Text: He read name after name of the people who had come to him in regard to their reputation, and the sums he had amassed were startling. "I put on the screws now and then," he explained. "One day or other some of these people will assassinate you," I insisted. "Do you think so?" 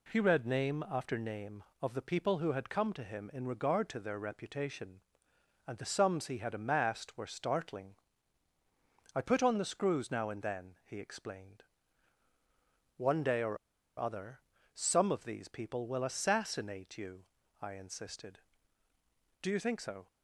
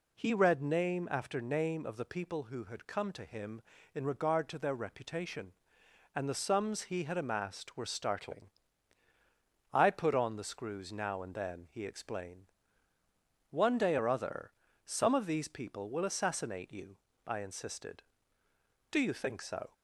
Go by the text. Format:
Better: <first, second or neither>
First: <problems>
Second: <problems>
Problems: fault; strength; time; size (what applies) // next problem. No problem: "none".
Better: second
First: pauses between "or" and "other"; at 13.5 s; 0.41 s long // pauses between "other" and "some"; slight; at 14.3 s; 0.34 s long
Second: pauses between "other" and "some"; slight; at 14.5 s; 0.34 s long